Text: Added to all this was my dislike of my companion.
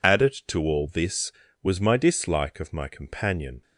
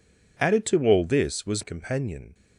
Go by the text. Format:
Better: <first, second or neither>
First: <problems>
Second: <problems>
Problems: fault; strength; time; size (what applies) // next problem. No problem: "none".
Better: first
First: none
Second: skips "my dislike of my"; at 1.6 s